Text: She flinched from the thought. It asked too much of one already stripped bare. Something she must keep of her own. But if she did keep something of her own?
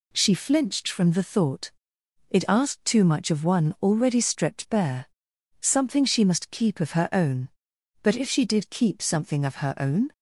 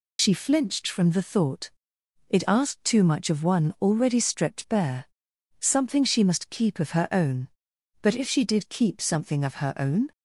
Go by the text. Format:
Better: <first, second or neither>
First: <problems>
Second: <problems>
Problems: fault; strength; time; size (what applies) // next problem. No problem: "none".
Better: first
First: none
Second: loses the start of "She"; at 0.1 s; 80 ms